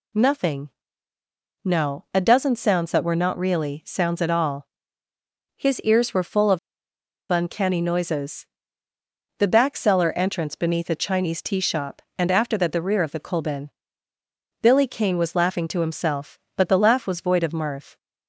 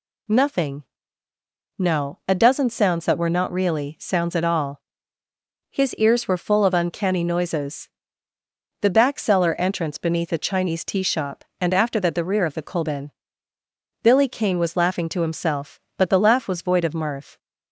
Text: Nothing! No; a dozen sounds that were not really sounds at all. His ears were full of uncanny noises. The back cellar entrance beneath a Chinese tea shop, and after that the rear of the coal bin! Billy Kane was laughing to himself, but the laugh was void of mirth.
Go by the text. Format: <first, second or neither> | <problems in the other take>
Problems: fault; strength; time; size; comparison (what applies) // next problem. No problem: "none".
second | pauses between "of" and "uncanny"; noticeable; at 6.5 s; 0.72 s long